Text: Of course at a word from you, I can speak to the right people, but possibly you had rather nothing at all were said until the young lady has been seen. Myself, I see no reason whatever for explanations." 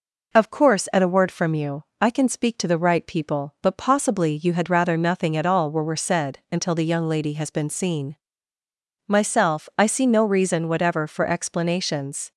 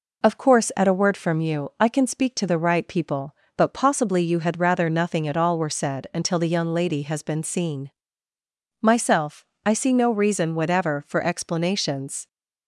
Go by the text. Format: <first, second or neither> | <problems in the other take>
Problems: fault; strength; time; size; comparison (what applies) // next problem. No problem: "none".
second | says "were" twice; at 5.8 s